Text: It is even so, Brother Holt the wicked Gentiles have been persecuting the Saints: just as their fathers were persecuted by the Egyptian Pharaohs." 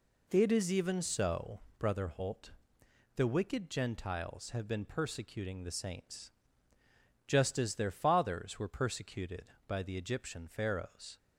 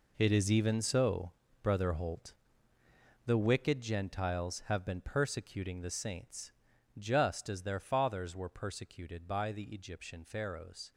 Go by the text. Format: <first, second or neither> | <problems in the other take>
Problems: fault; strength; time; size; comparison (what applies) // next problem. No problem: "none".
first | gets quieter; strong; throughout; 12 dB // pauses between "Holt" and "the"; noticeable; at 2.3 s; 0.92 s long; noticeable in the first